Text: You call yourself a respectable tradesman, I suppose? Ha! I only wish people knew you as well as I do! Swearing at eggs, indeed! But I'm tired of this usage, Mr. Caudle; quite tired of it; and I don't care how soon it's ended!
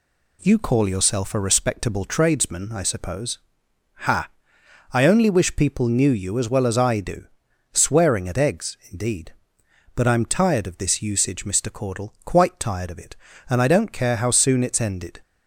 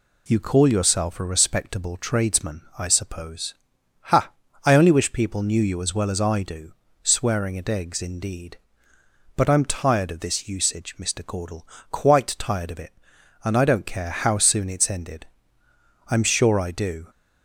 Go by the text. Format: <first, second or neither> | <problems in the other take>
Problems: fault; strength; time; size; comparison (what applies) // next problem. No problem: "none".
first | goes on to say "I'm sure I do"; noticeable; from 16.0 s on; 0.98 s long